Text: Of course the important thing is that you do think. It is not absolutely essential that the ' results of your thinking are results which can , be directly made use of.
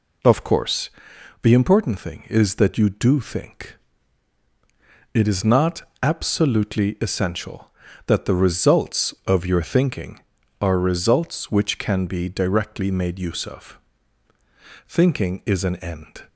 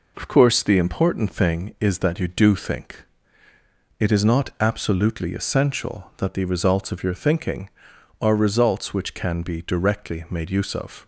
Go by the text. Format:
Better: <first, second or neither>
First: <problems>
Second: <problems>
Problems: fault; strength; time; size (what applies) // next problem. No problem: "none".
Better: second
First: pauses between "course" and "the"; noticeable; at 0.8 s; 0.52 s long // pauses between "not" and "absolutely"; slight; at 5.8 s; 0.20 s long // goes on to say "Thinking is an end"; from 14.9 s on; 1.3 s long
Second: none